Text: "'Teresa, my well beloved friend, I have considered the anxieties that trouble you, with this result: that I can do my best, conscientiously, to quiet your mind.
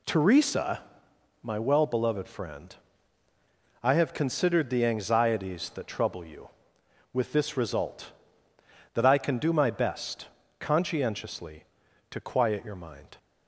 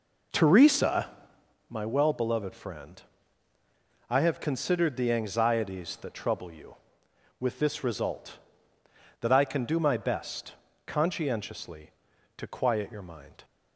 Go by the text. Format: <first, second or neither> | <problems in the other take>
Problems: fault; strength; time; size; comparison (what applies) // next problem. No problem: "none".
first | starts louder than the rest; noticeable; until 1.6 s; 4.5 dB